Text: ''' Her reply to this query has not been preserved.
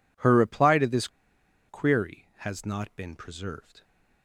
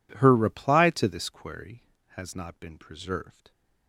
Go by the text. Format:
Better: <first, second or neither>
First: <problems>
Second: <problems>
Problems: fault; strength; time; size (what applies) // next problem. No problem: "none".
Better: second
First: pauses between "this" and "query"; noticeable; at 1.0 s; 0.60 s long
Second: none